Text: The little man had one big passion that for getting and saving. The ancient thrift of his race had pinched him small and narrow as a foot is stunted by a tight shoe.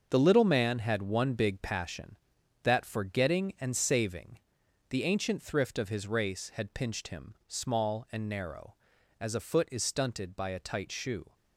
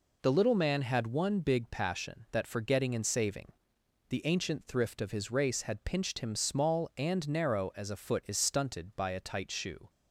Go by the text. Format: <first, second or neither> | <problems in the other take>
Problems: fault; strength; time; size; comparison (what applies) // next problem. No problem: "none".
second | gets quieter; strong; throughout; 9.5 dB